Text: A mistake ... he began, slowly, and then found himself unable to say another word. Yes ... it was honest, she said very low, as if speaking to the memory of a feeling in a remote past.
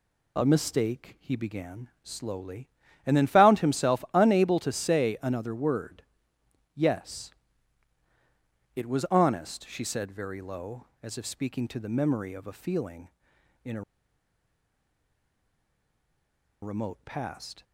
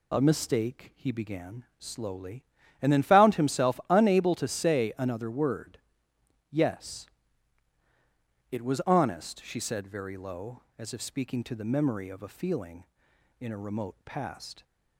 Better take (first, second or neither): second